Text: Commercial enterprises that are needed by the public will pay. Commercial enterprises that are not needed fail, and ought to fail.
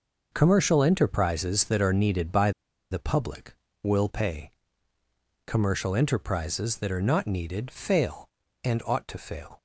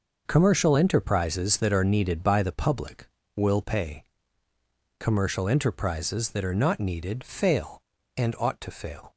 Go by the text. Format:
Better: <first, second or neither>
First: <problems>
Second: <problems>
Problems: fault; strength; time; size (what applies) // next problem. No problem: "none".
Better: second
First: pauses between "by" and "the"; at 2.5 s; 0.40 s long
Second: none